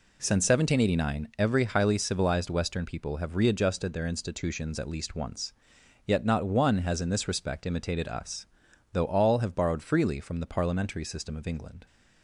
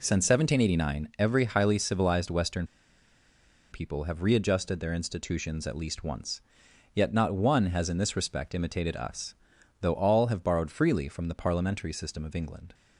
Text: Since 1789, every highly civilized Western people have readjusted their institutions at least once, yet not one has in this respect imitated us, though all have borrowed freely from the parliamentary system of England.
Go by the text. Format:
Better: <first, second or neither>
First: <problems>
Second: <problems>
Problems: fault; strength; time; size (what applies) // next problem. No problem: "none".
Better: first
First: none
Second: pauses between "Western" and "people"; at 2.6 s; 1.0 s long